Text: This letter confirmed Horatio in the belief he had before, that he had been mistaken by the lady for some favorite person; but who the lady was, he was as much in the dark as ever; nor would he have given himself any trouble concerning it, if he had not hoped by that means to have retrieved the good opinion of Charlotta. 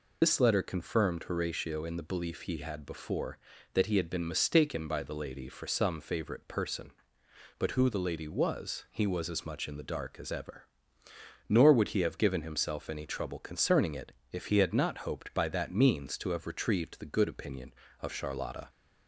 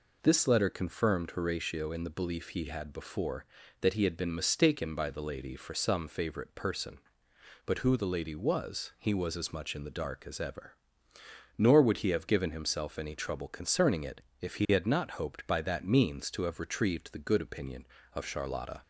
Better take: second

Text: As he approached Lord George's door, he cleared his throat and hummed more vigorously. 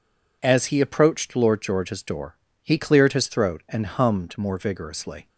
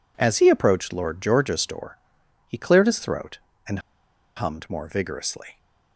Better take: first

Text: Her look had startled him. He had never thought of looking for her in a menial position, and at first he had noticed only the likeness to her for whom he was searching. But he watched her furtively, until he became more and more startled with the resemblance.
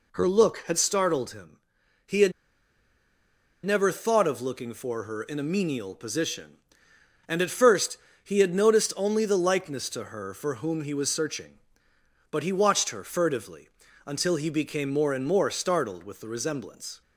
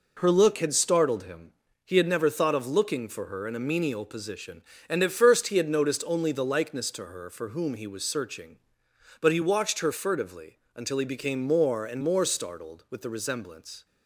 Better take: second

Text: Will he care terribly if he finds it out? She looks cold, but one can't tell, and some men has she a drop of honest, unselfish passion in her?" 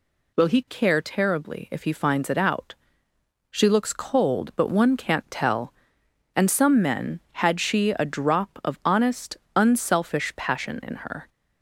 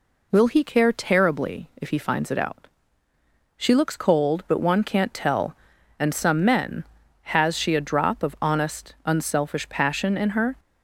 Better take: second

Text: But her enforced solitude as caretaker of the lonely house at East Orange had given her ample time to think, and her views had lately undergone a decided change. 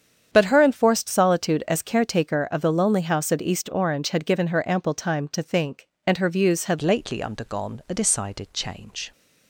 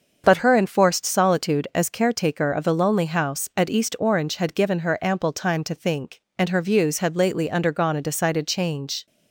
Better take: second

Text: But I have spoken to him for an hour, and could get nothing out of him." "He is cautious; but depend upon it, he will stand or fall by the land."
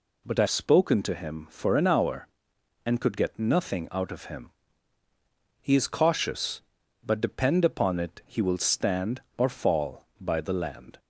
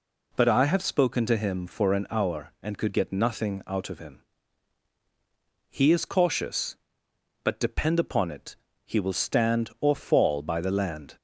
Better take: second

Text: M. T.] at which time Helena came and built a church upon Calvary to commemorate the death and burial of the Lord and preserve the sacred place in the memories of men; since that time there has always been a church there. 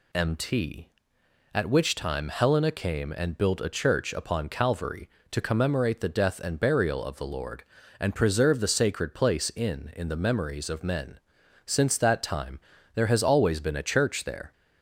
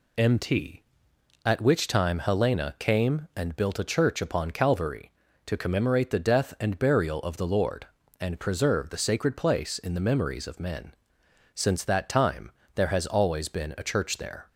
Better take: second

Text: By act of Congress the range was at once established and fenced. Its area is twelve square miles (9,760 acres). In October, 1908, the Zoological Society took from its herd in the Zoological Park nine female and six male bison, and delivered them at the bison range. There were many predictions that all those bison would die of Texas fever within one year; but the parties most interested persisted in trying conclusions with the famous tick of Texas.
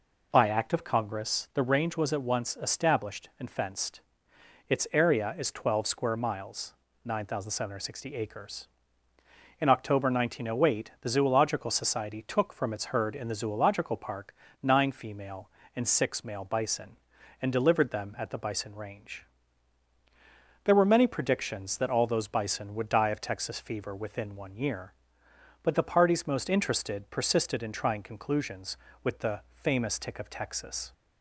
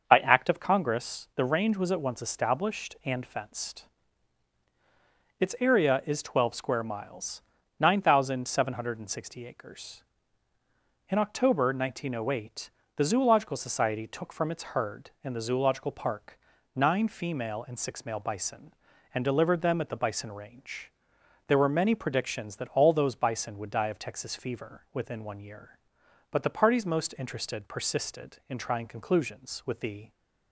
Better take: first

